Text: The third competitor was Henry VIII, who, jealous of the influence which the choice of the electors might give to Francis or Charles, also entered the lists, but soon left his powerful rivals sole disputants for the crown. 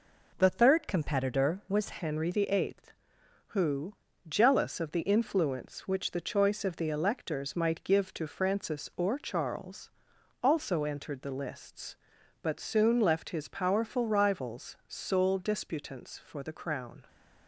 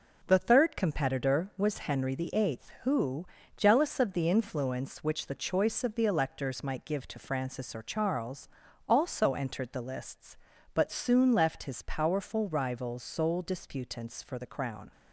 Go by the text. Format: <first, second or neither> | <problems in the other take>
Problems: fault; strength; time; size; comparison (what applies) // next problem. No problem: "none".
second | changes voice at "Henry"; from 1.9 s on; 15.1 s long